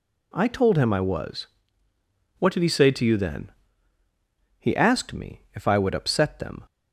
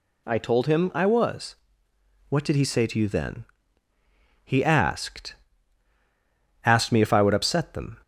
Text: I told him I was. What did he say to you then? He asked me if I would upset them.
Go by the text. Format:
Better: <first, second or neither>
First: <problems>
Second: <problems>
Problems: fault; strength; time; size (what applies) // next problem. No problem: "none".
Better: first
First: none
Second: says "asked" twice; at 6.6 s